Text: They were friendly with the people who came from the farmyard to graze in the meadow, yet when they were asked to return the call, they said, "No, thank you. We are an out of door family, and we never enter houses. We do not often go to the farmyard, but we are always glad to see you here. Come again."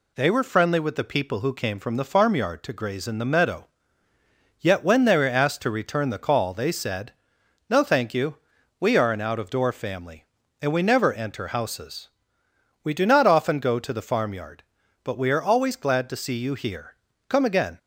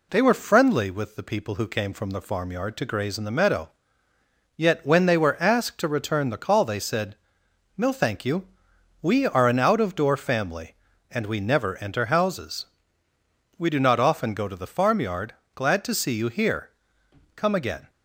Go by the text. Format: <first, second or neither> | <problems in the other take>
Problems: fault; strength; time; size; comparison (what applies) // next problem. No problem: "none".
first | skips "but we are always"; at 15.4 s